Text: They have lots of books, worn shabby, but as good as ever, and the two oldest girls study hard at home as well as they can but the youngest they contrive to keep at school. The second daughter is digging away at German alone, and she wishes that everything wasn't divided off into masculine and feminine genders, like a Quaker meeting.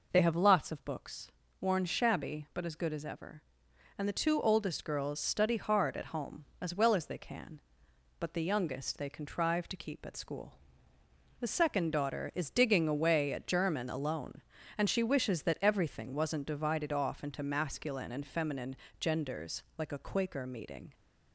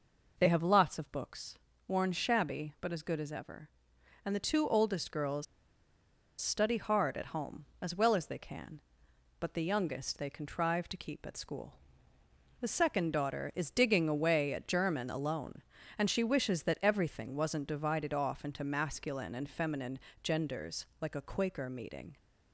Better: first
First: pauses between "feminine" and "genders"; slight; at 18.7 s; 0.24 s long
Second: pauses between "girls" and "study"; noticeable; at 5.4 s; 0.95 s long // pauses between "feminine" and "genders"; slight; at 20.0 s; 0.24 s long

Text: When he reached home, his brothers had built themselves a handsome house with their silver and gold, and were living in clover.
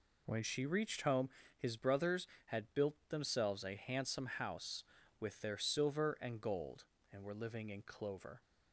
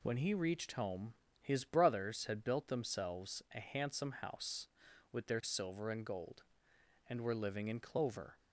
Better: second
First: says "she" for "he"; at 0.4 s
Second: none

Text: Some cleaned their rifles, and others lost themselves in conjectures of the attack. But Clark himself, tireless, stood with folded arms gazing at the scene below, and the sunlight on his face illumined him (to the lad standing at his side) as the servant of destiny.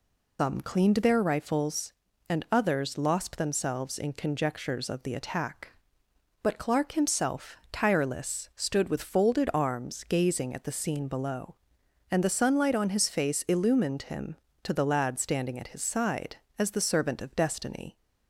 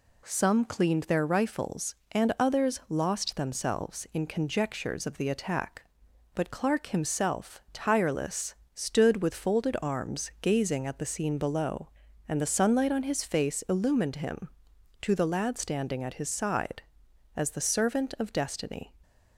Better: second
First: loses the start of "Some"; at 0.3 s; 150 ms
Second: none

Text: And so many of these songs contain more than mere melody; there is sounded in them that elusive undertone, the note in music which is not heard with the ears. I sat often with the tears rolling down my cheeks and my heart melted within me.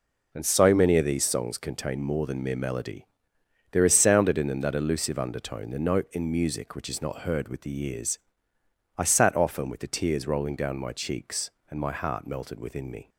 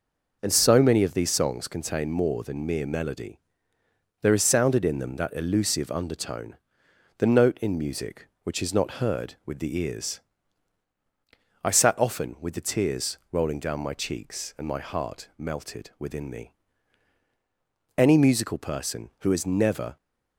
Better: first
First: none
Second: pauses between "tears" and "rolling"; slight; at 13.1 s; 0.16 s long // goes on to say "Any musical person who has never"; strong; from 17.9 s on; 1.9 s long

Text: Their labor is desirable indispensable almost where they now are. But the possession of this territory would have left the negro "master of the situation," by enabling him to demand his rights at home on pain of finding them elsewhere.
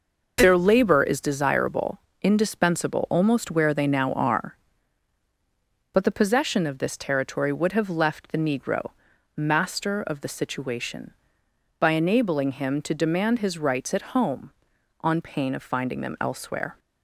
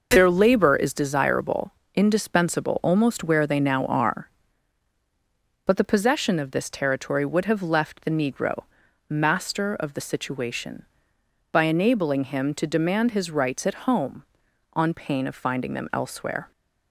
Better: neither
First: pauses between "desirable" and "indispensable"; slight; at 1.9 s; 0.22 s long // pauses between "negro" and "master"; at 8.9 s; 0.44 s long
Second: pauses between "desirable" and "indispensable"; slight; at 1.7 s; 0.22 s long // pauses between "negro" and "master"; at 8.6 s; 0.44 s long

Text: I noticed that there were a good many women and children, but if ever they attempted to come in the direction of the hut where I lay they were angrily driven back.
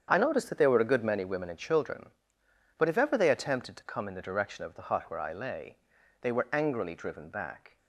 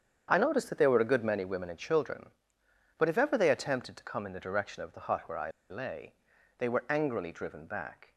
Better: first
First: starts louder than the rest; strong; until 1.1 s; 8 dB // pauses between "lay" and "they"; at 5.7 s; 0.44 s long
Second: starts louder than the rest; strong; until 1.3 s; 8 dB // pauses between "I" and "lay"; slight; at 5.4 s; 0.20 s long // pauses between "lay" and "they"; at 6.1 s; 0.44 s long

